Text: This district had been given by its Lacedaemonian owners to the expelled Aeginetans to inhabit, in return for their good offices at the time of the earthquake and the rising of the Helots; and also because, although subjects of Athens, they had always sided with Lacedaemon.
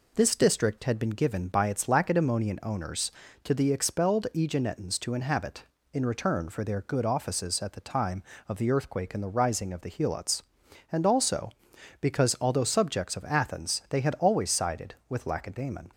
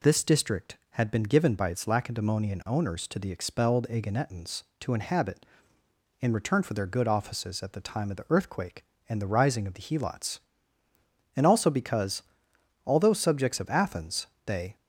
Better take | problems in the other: first | stops before "had always sided with Lacedaemon"; at 14.7 s

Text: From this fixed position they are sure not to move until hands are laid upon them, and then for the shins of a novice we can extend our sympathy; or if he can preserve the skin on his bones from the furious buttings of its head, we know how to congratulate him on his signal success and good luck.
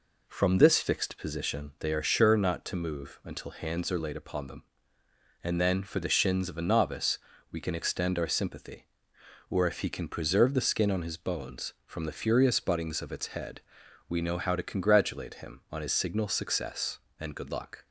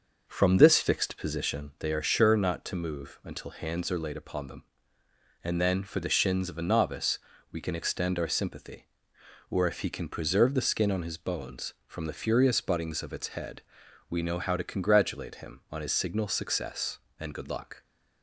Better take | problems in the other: first | starts louder than the rest; until 1.6 s; 6 dB // pauses between "novice" and "we"; slight; at 7.1 s; 0.32 s long; slight in the first

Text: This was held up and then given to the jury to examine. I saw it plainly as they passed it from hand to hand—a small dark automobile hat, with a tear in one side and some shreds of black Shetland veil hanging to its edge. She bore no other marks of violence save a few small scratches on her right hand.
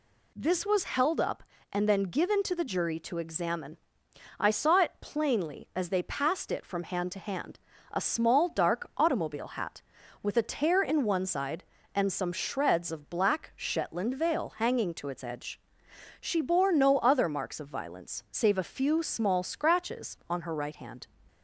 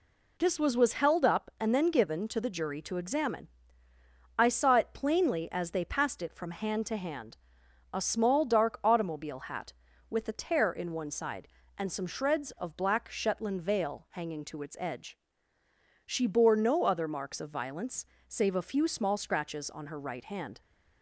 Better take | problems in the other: first | says "was" twice; at 0.7 s // pauses between "violence" and "save"; slight; at 18.0 s; 0.24 s long

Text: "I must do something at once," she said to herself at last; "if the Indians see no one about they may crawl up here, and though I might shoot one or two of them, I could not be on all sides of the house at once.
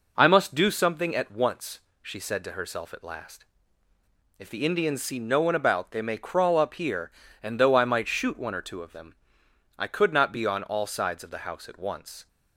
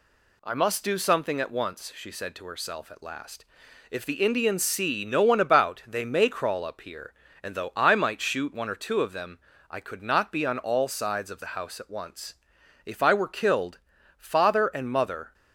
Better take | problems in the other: first | goes on to say "If I were killed father and mother"; strong; from 12.8 s on; 2.4 s long

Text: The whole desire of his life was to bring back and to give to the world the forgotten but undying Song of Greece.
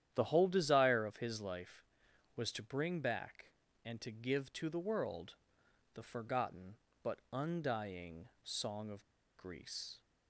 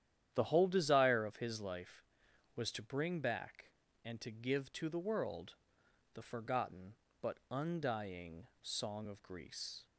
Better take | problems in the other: second | starts louder than the rest; strong; until 1.1 s; 10.5 dB; strong in the second // pauses between "world" and "the"; noticeable; at 5.3 s; 0.58 s long; noticeable in the second // pauses between "undying" and "Song"; slight; at 8.2 s; 0.16 s long; slight in the second // pauses between "of" and "Greece"; slight; at 9.0 s; 0.34 s long

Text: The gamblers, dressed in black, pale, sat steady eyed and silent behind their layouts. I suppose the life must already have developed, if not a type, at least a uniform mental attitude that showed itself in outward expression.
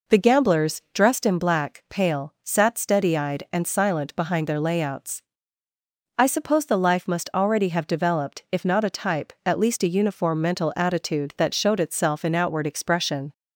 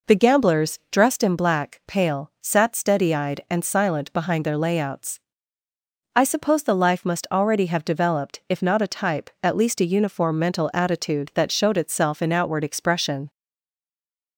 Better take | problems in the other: first | stays silent after the last word; from 13.2 s on; 1.1 s long

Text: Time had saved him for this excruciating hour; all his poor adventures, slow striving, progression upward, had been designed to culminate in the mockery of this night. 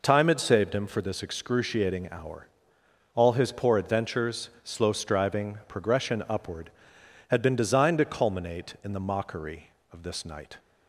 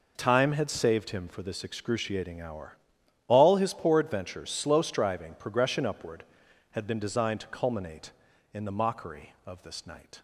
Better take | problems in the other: neither | none

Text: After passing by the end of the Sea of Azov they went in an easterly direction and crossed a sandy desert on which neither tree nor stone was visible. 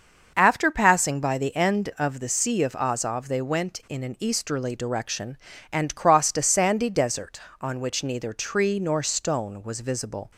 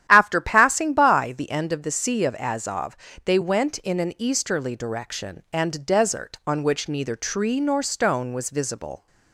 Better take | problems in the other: first | starts louder than the rest; strong; until 1.1 s; 11 dB; also in the first // pauses between "Azov" and "they"; slight; at 2.9 s; 0.30 s long // skips "crossed a sandy"; at 5.8 s

